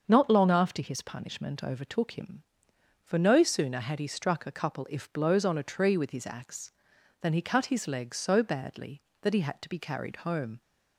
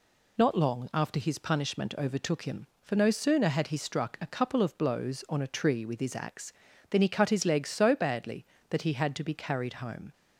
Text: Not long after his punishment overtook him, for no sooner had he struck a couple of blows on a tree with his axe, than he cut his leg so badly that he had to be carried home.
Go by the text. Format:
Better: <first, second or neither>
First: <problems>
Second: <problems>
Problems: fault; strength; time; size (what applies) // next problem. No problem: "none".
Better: second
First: starts louder than the rest; until 1.0 s; 6.5 dB // says "if" for "of"; at 4.9 s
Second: none